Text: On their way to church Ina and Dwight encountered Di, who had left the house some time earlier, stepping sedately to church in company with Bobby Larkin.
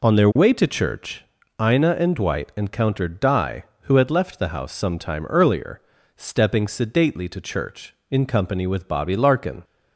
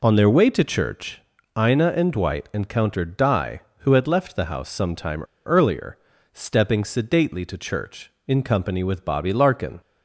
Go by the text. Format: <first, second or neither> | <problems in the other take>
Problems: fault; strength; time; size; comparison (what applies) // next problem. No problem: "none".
first | pauses between "church" and "Ina"; at 1.2 s; 0.38 s long; also in the first // pauses between "time" and "earlier"; slight; at 5.2 s; 0.25 s long